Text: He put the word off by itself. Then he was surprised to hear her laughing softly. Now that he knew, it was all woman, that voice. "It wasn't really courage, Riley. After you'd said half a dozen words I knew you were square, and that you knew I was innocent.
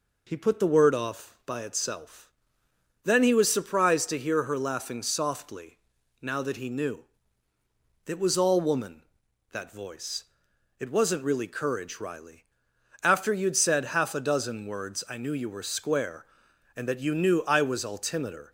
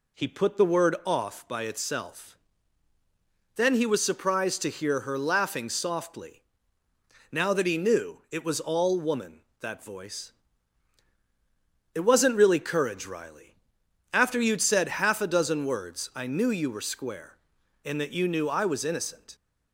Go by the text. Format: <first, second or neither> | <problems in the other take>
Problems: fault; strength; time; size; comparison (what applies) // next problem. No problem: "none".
second | says "altimeter" for "innocent"; at 17.8 s